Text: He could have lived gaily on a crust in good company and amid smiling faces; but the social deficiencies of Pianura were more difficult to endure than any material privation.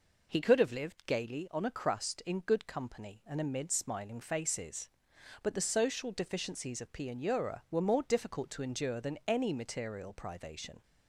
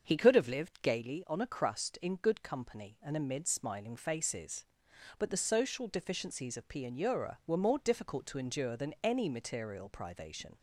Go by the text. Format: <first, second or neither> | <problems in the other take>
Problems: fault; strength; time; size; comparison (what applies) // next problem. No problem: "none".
first | starts louder than the rest; until 1.0 s; 7 dB